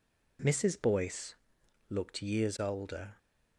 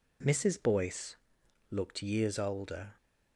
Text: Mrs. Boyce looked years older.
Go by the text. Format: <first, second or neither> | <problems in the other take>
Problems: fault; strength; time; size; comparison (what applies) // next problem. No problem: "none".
neither | pauses between "Boyce" and "looked"; noticeable; the same in both